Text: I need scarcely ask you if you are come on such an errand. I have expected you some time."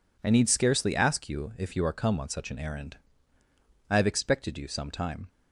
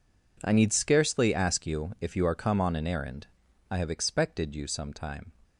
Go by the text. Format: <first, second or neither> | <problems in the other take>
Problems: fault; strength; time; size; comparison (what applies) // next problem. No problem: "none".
first | skips "such"; at 2.7 s